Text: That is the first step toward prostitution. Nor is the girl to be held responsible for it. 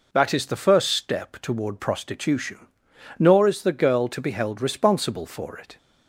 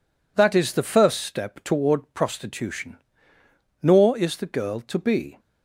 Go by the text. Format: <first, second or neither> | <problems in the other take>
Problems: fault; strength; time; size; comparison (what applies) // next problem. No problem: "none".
first | stops before "held responsible for it"; at 5.3 s